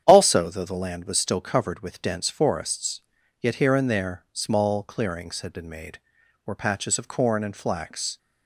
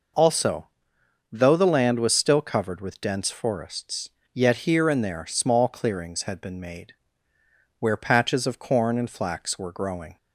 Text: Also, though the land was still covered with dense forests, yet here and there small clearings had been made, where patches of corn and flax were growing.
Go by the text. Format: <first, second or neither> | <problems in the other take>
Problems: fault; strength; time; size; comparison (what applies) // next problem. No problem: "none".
second | starts louder than the rest; strong; until 1.0 s; 9 dB // stops before "were growing"; at 8.1 s